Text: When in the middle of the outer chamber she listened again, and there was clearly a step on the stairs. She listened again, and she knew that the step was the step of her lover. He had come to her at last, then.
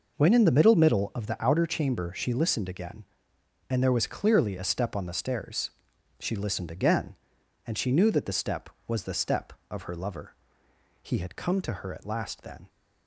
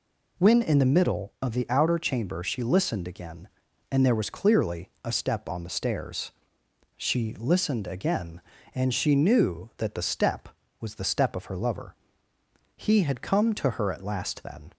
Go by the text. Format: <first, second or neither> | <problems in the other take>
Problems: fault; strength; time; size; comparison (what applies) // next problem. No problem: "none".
second | says "middle" twice; at 0.7 s